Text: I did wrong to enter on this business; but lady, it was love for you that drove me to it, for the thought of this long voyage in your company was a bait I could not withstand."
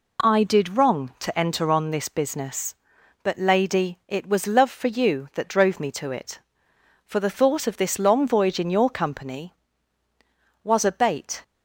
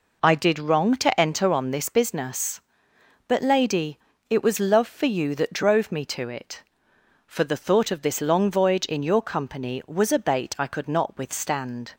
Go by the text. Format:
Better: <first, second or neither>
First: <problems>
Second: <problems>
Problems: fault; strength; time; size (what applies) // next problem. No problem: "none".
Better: second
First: stops before "I could not withstand"; at 11.4 s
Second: none